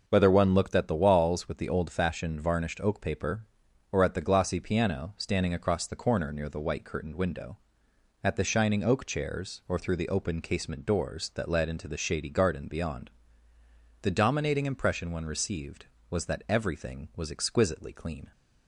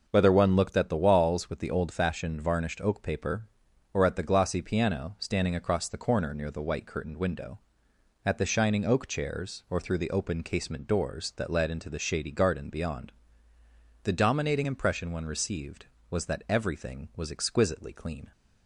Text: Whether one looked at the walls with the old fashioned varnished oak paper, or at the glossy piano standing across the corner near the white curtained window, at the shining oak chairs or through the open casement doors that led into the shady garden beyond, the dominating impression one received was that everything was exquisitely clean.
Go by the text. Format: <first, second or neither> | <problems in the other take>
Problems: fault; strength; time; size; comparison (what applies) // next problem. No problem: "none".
neither | none